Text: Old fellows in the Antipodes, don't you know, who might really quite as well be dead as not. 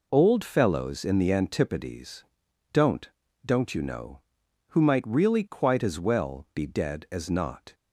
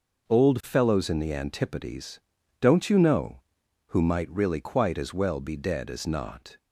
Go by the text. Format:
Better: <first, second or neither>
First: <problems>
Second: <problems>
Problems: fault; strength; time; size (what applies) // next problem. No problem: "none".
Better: second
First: says "don't" twice; at 3.4 s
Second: none